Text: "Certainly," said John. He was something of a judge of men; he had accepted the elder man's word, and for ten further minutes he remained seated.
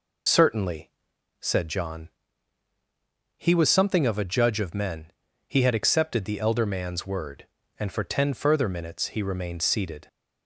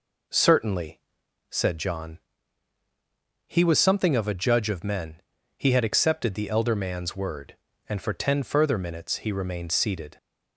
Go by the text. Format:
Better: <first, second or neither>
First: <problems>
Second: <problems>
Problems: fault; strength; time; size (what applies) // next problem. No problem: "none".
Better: second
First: loses the start of "Certainly"; at 0.2 s; 70 ms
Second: none